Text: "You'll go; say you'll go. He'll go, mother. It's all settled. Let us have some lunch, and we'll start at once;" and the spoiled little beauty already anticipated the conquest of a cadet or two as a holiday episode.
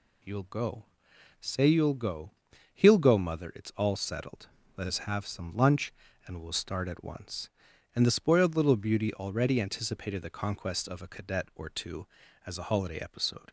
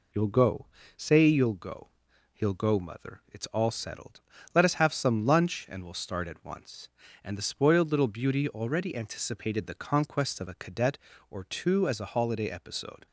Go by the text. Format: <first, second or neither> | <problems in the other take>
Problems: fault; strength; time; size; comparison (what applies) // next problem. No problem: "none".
neither | none